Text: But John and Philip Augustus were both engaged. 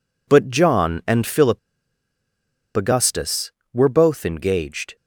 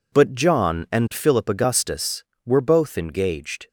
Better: second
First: pauses between "Philip" and "Augustus"; at 1.5 s; 1.1 s long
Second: none

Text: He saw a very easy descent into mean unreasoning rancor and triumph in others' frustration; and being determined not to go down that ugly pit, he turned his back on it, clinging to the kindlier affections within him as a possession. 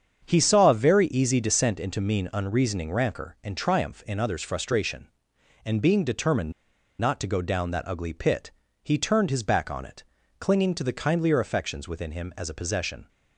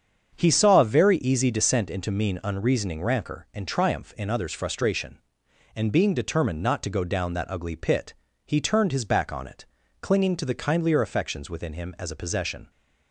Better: second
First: starts louder than the rest; strong; until 1.2 s; 7.5 dB // pauses between "determined" and "not"; noticeable; at 6.5 s; 0.47 s long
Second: starts louder than the rest; strong; until 1.3 s; 7.5 dB

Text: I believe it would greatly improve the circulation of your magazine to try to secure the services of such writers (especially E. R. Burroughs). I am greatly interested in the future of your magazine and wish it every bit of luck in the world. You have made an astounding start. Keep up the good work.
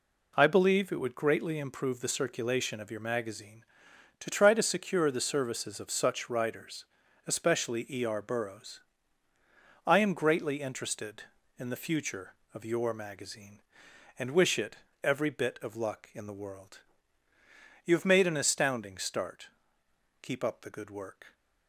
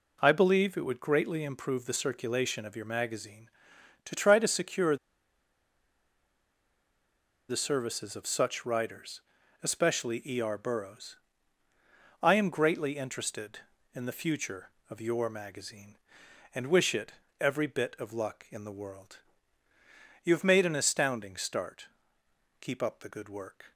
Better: first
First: pauses between "it" and "every"; slight; at 14.7 s; 0.27 s long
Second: pauses between "secure" and "the"; strong; at 4.9 s; 2.5 s long // pauses between "it" and "every"; slight; at 17.1 s; 0.28 s long

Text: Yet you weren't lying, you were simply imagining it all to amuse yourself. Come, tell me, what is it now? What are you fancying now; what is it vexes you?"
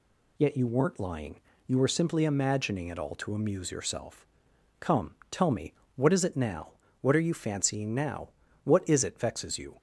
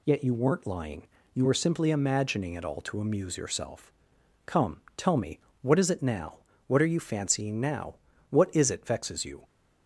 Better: neither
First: none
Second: none

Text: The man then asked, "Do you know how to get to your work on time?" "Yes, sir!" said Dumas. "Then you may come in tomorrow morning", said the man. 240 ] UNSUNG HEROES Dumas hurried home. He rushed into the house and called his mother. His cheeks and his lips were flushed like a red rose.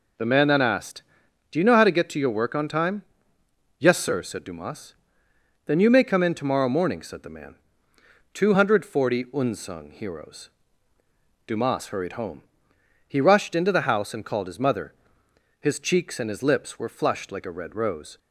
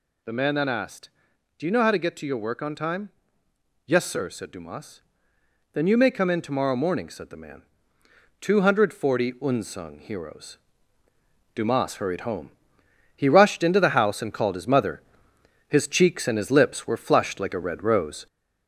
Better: first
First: pauses between "HEROES" and "Dumas"; noticeable; at 10.5 s; 0.96 s long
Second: gets louder; slight; throughout; 3 dB // pauses between "HEROES" and "Dumas"; noticeable; at 10.5 s; 0.96 s long

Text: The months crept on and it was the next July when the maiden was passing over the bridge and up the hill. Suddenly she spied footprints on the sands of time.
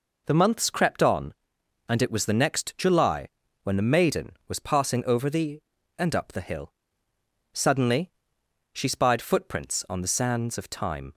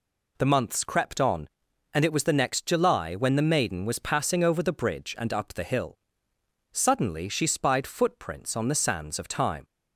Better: second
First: pauses between "July" and "when"; slight; at 3.2 s; 0.36 s long // skips "bridge"; at 5.7 s // pauses between "Suddenly" and "she"; noticeable; at 8.1 s; 0.62 s long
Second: none

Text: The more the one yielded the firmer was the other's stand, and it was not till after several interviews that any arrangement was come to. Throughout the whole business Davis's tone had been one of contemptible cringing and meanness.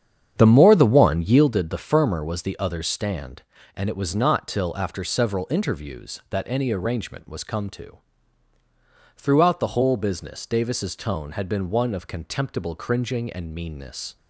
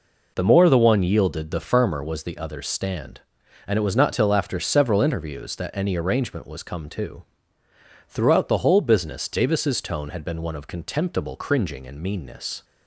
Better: second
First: starts louder than the rest; strong; until 1.5 s; 8.5 dB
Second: none

